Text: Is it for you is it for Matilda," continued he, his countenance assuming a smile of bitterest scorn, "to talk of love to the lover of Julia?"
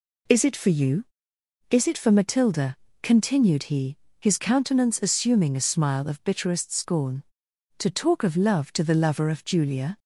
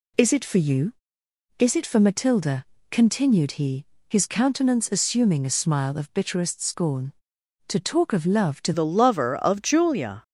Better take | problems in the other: first | changes voice at "the"; from 8.7 s on; 1.5 s long

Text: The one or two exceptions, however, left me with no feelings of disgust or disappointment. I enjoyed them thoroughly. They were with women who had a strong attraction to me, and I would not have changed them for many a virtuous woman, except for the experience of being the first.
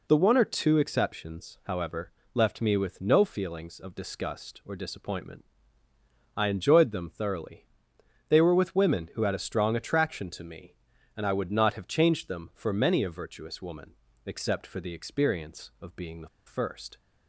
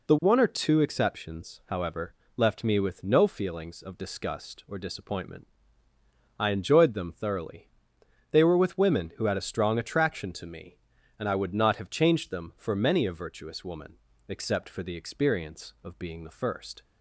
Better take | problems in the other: second | pauses between "the" and "first"; slight; at 16.2 s; 0.19 s long

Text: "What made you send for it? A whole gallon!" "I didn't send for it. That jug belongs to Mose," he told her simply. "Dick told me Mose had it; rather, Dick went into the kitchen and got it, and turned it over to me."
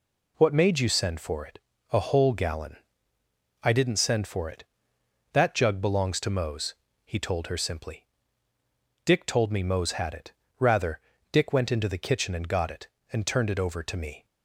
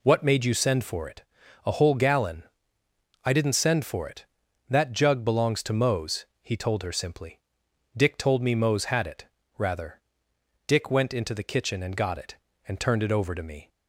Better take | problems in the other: neither | none

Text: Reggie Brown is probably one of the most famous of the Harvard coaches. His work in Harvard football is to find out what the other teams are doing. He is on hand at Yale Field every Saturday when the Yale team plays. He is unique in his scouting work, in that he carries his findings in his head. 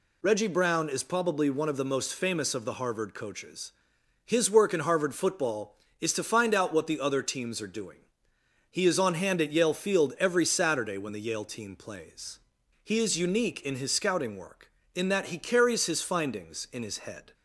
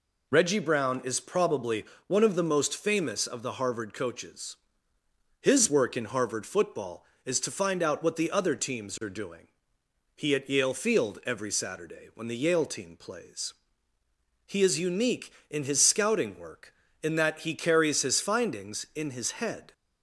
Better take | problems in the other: first | pauses between "probably" and "one"; slight; at 1.8 s; 0.22 s long // skips "is on hand"; at 10.3 s

